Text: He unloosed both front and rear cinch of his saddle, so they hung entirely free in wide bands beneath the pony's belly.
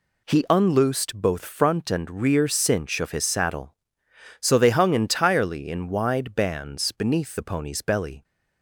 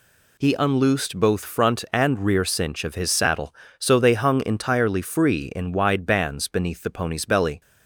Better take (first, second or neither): second